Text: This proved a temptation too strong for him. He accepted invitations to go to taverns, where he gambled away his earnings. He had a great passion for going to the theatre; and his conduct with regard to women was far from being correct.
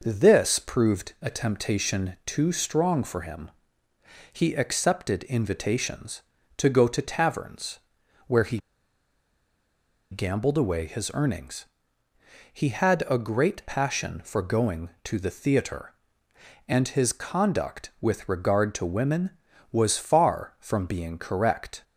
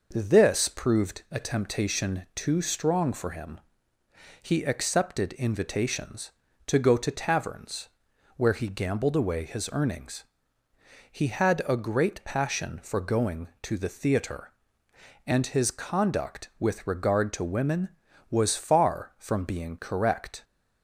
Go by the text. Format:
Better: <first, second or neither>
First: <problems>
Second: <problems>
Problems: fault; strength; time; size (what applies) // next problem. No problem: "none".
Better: second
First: pauses between "he" and "gambled"; strong; at 8.5 s; 1.5 s long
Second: none